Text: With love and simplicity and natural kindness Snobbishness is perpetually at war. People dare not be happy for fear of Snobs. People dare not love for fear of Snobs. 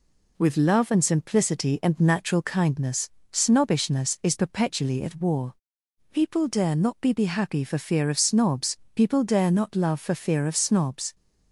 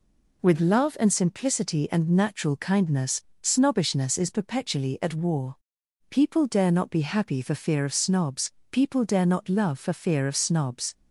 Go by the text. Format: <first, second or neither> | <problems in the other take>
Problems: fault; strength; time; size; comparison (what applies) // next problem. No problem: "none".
second | pauses between "kindness" and "Snobbishness"; slight; at 3.0 s; 0.22 s long; slight in the second // says "be" twice; at 7.1 s